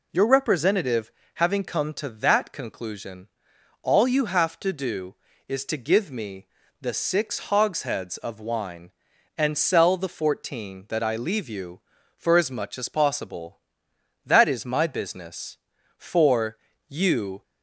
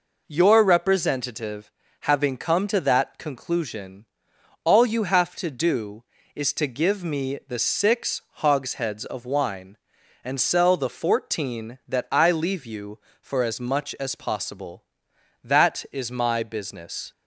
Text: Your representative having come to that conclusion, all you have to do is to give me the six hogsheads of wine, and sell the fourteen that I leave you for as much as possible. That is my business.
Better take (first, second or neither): second